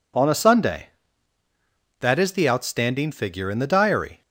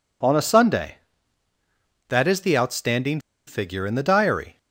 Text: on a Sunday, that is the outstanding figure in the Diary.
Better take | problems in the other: first | pauses between "outstanding" and "figure"; slight; at 3.1 s; 0.27 s long

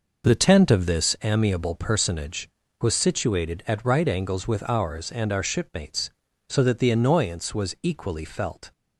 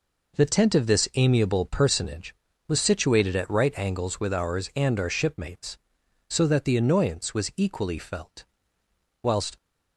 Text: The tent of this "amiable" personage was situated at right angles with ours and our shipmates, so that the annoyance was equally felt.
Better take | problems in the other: first | goes on to say "Whilst"; slight; from 9.2 s on; 0.34 s long

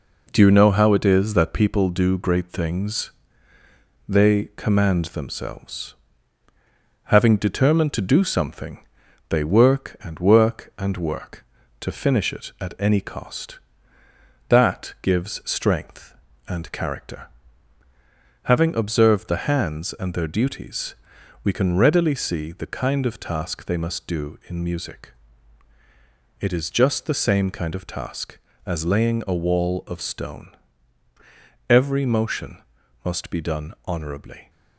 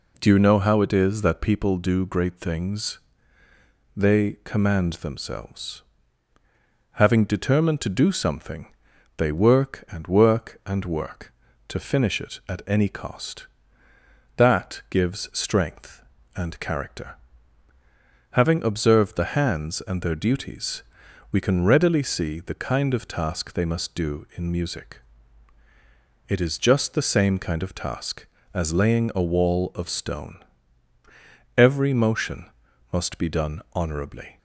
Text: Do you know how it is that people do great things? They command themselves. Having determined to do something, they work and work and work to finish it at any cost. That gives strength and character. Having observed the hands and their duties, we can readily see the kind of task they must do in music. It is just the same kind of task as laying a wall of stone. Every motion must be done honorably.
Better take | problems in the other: second | gets quieter; noticeable; throughout; 4.5 dB // pauses between "motion" and "must"; at 32.6 s; 0.42 s long; also in the second

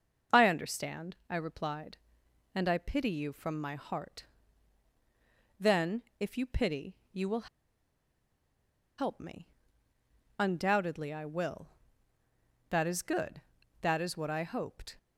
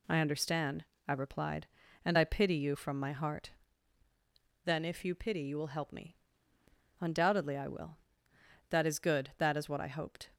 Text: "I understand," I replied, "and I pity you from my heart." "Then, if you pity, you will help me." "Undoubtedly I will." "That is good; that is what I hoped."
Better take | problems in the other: second | starts louder than the rest; until 1.4 s; 6.5 dB // pauses between "will" and "help"; strong; at 7.4 s; 1.5 s long

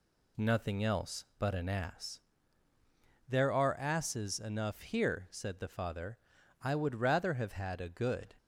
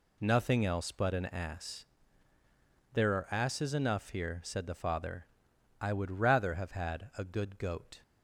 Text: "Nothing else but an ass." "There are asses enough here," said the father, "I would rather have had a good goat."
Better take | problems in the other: second | stops before "goat"; at 8.3 s

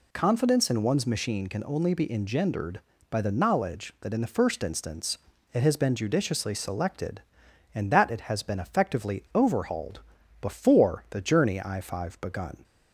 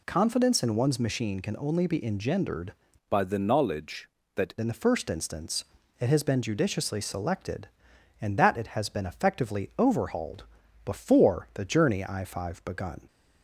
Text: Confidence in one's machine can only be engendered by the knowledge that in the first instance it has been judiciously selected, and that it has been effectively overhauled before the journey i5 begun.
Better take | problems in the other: first | changes voice from "by" to "that"; from 3.0 to 4.5 s; 1.5 s long // pauses between "instance" and "it"; slight; at 5.6 s; 0.34 s long; slight in the first // pauses between "overhauled" and "before"; at 10.4 s; 0.40 s long; also in the first

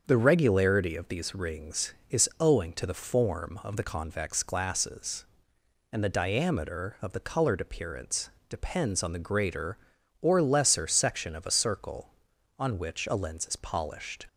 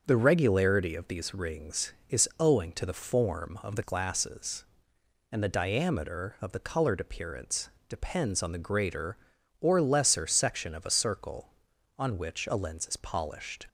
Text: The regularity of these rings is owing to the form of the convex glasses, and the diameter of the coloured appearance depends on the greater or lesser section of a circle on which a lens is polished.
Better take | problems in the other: first | starts louder than the rest; until 1.0 s; 6.5 dB; also in the first // skips "convex"; at 3.8 s // pauses between "appearance" and "depends"; slight; at 7.6 s; 0.22 s long; slight in the first

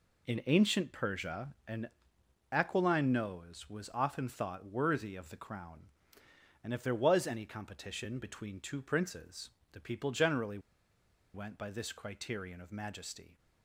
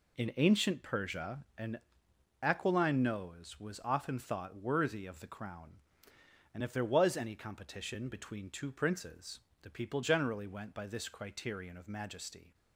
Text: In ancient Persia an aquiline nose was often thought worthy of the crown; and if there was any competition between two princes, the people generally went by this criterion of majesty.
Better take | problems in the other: second | pauses between "Persia" and "an"; slight; at 1.4 s; 0.18 s long; slight in the second // pauses between "an" and "aquiline"; noticeable; at 1.8 s; 0.62 s long; noticeable in the second // pauses between "generally" and "went"; noticeable; at 10.5 s; 0.74 s long

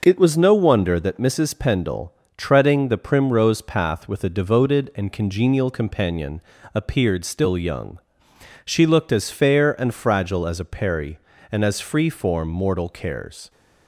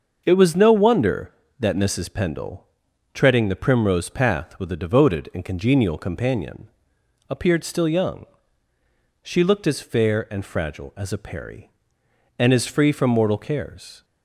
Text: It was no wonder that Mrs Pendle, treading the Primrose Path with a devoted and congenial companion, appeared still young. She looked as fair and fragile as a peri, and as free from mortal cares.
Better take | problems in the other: second | starts louder than the rest; noticeable; until 1.0 s; 6 dB; also in the second // says "form" for "from"; at 12.0 s

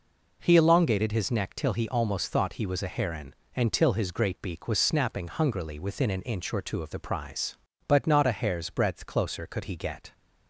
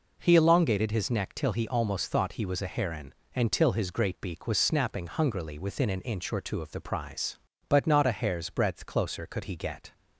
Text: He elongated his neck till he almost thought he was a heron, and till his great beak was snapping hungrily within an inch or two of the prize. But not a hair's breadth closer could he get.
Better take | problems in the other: neither | none

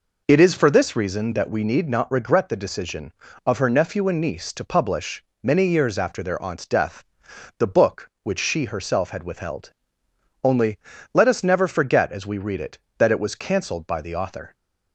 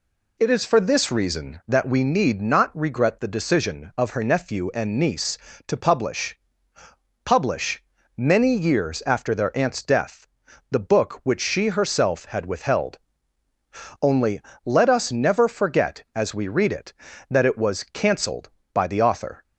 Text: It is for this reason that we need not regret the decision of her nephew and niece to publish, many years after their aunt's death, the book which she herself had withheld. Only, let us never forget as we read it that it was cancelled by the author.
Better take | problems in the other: first | says "publish" twice; at 7.2 s

